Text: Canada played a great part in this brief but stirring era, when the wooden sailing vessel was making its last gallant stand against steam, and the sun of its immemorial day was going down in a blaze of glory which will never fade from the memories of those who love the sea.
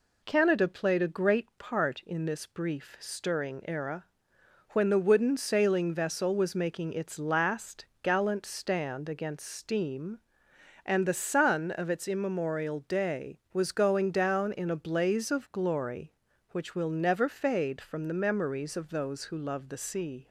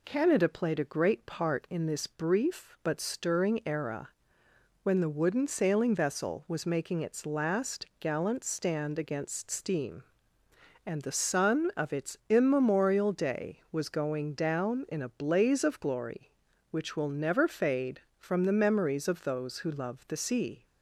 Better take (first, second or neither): second